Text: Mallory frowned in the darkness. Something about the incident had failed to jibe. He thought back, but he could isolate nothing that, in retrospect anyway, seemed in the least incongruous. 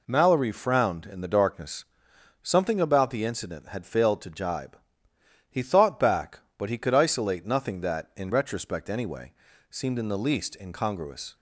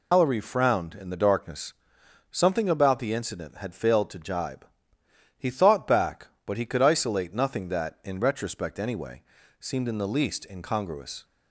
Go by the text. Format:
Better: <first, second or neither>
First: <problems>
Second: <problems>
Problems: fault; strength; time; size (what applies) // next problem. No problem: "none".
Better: first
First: none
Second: loses the start of "Mallory"; at 0.1 s; 160 ms